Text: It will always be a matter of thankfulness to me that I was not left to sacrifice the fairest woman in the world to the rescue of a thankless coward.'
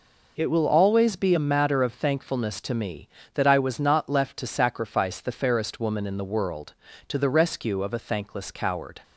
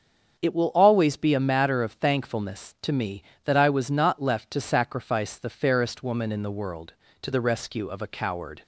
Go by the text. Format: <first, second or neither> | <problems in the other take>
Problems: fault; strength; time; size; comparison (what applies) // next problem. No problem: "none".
first | starts louder than the rest; strong; until 1.4 s; 7 dB // skips "thankless"; at 8.0 s